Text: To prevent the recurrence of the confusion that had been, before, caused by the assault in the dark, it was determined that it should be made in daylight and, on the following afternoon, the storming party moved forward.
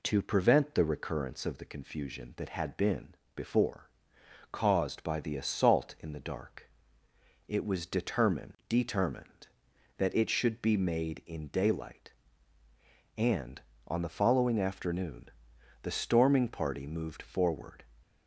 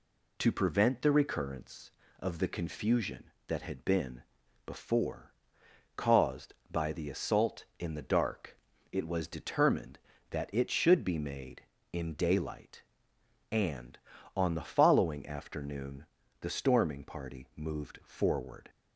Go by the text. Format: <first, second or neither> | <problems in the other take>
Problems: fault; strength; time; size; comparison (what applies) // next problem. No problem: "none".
second | says "determined" twice; at 8.6 s